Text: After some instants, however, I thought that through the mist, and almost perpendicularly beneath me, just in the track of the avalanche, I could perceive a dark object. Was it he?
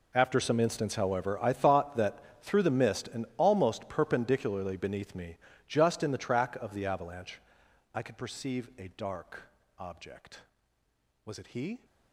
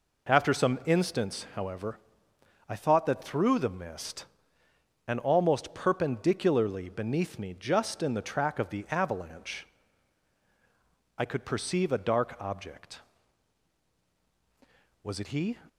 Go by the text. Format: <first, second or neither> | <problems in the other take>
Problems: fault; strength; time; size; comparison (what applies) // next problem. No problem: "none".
second | gets quieter; strong; throughout; 17.5 dB // pauses between "that" and "through"; slight; at 2.1 s; 0.22 s long // pauses between "dark" and "object"; slight; at 9.4 s; 0.34 s long